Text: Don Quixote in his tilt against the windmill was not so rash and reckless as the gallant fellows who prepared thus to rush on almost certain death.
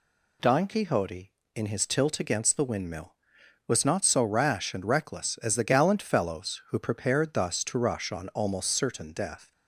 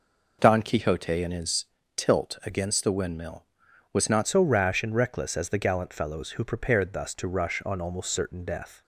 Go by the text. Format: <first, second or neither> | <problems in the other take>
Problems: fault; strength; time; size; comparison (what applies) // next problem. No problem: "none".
first | pauses between "his" and "tilt"; slight; at 1.6 s; 0.32 s long // changes voice at "so"; from 4.2 s on; 4.6 s long